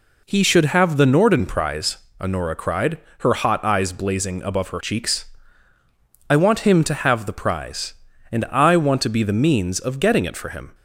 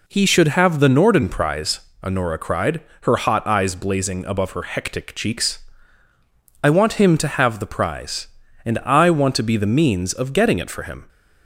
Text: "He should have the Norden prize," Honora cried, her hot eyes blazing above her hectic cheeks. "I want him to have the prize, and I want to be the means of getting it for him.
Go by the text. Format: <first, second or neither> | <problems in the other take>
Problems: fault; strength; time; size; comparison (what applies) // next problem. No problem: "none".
second | skips "hectic"; at 4.8 s